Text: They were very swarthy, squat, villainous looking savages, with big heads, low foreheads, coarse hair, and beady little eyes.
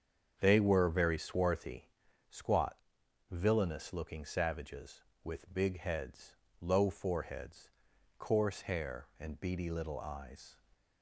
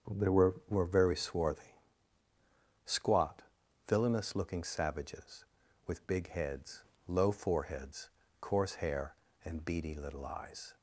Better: first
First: starts louder than the rest; strong; until 1.3 s; 7 dB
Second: starts louder than the rest; strong; until 1.2 s; 7 dB // says "were" twice; at 0.6 s

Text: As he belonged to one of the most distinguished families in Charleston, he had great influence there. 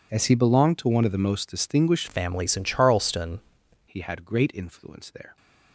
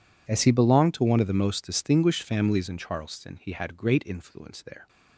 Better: second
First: changes voice from "families" to "Charleston"; from 2.0 to 3.3 s; 1.3 s long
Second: none

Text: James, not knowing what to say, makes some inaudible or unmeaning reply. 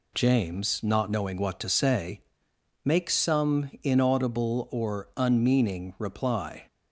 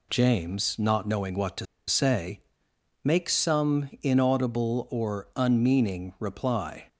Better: first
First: none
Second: pauses between "to" and "say"; slight; at 1.6 s; 0.22 s long

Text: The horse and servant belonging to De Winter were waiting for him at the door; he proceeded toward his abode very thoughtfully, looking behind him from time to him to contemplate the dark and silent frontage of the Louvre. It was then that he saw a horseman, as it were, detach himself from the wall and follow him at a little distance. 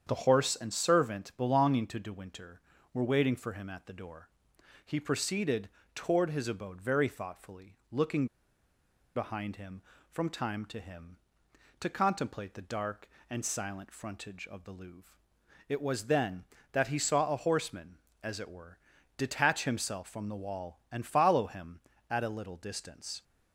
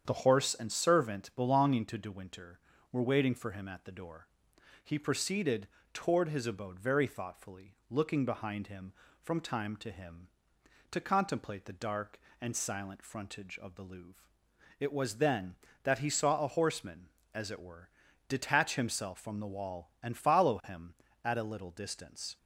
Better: second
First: starts louder than the rest; strong; until 1.0 s; 8 dB // pauses between "proceeded" and "toward"; slight; at 5.6 s; 0.26 s long // pauses between "looking" and "behind"; noticeable; at 8.2 s; 0.90 s long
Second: starts louder than the rest; strong; until 1.0 s; 8 dB // pauses between "proceeded" and "toward"; slight; at 5.6 s; 0.26 s long

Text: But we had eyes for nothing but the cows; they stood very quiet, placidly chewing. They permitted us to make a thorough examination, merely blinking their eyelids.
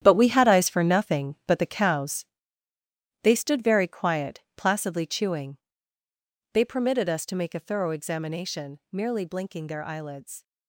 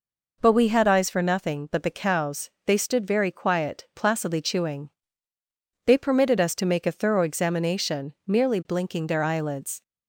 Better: second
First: gets quieter; strong; throughout; 11 dB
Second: none

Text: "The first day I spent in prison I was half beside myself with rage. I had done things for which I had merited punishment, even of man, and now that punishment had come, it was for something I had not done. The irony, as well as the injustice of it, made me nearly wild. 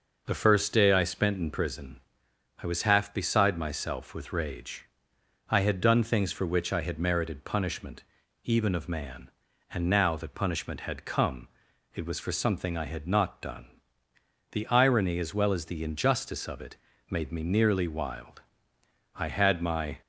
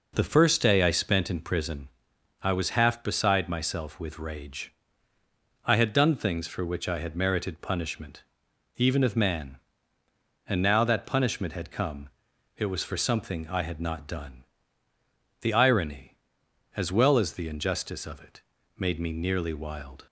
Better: second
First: pauses between "prison" and "I"; noticeable; at 1.9 s; 0.60 s long // goes on to say "I had my"; noticeable; from 19.1 s on; 0.86 s long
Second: pauses between "prison" and "I"; noticeable; at 1.8 s; 0.52 s long

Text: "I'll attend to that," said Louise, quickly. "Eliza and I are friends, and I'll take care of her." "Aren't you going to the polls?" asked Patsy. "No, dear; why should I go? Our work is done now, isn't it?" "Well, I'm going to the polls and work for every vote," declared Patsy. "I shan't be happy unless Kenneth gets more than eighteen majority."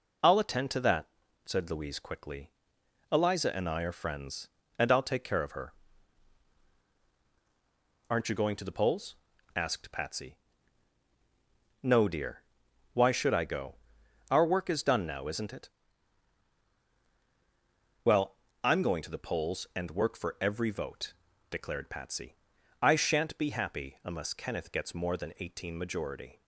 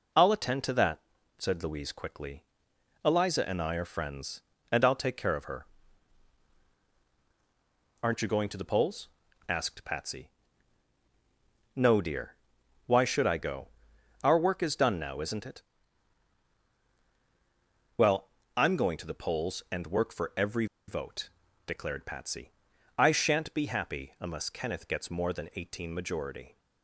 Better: first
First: none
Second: pauses between "every" and "vote"; slight; at 20.6 s; 0.22 s long

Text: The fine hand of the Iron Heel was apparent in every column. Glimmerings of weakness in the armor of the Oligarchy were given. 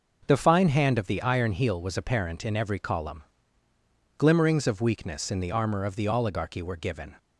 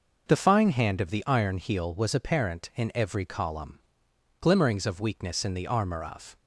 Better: first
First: none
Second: stops before "the Oligarchy were given"; at 6.3 s

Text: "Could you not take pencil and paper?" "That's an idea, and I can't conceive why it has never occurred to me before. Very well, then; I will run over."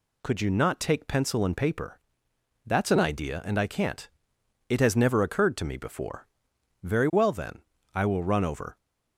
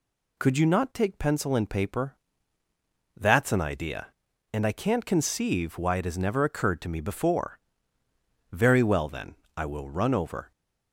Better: second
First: skips "conceive why"; at 4.3 s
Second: none

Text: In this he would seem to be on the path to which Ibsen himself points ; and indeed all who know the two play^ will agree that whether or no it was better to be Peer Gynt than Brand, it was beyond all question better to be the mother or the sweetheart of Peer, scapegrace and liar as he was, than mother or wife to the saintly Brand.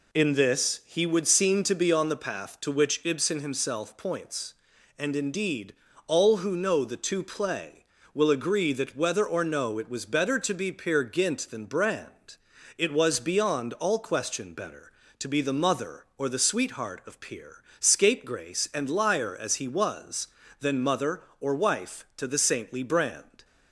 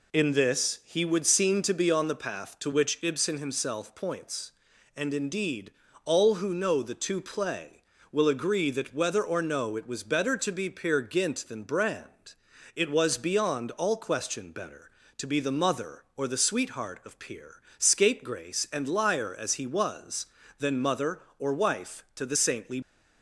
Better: first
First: pauses between "indeed" and "all"; slight; at 5.7 s; 0.32 s long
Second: pauses between "indeed" and "all"; slight; at 5.7 s; 0.32 s long // stops before "Brand"; at 22.8 s

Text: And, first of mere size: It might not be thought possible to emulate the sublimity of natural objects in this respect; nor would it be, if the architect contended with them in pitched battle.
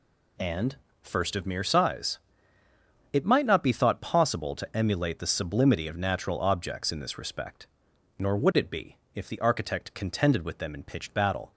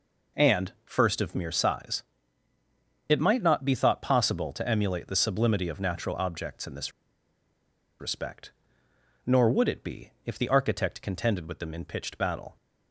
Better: first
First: none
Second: pauses between "this" and "respect"; at 6.9 s; 1.0 s long

